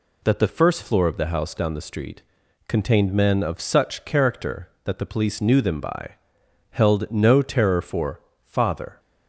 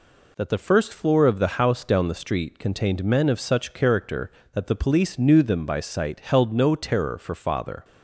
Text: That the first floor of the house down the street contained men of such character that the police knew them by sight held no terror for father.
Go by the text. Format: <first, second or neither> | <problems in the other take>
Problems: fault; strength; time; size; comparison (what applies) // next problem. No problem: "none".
second | pauses between "street" and "contained"; noticeable; at 2.2 s; 0.46 s long // skips "sight"; at 6.4 s // pauses between "for" and "father"; slight; at 8.2 s; 0.24 s long